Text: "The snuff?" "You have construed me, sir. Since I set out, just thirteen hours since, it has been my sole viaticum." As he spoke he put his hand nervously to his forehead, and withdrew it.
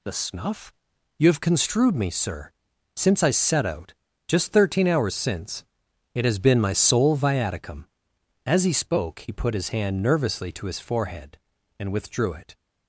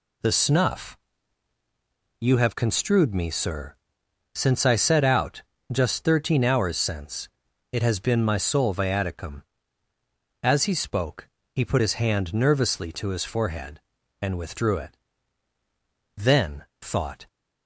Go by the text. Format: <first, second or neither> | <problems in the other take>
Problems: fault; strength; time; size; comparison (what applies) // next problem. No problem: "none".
first | pauses between "spoke" and "he"; slight; at 11.2 s; 0.28 s long // goes on to say "Then thought"; noticeable; from 16.1 s on; 1.1 s long